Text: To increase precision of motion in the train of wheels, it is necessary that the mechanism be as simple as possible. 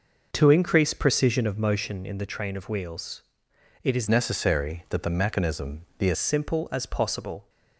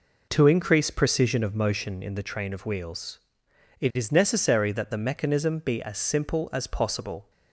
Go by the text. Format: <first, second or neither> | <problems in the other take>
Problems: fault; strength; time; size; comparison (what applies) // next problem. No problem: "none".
second | changes voice from "necessary" to "as"; from 4.0 to 6.1 s; 2.1 s long // pauses between "mechanism" and "be"; slight; at 5.8 s; 0.16 s long